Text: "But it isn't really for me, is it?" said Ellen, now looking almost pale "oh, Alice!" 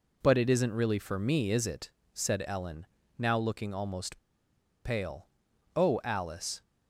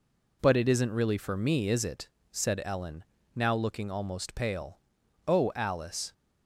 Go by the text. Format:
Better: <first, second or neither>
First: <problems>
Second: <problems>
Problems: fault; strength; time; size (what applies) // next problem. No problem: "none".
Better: second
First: pauses between "almost" and "pale"; noticeable; at 4.1 s; 0.67 s long // pauses between "pale" and "oh"; noticeable; at 5.2 s; 0.48 s long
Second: pauses between "pale" and "oh"; noticeable; at 4.7 s; 0.48 s long